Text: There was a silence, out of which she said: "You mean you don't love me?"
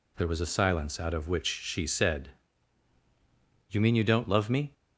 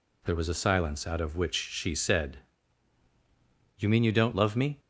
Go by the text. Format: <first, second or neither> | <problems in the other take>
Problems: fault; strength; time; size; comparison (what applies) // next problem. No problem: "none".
neither | none